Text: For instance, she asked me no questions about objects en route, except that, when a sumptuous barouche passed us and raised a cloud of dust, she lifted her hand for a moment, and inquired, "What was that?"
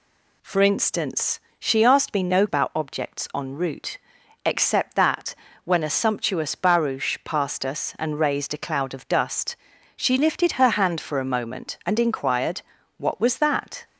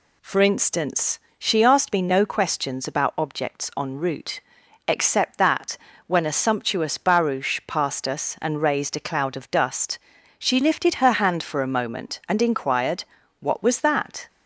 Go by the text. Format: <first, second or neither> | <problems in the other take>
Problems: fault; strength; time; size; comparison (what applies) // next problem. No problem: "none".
second | skips "questions"; at 2.4 s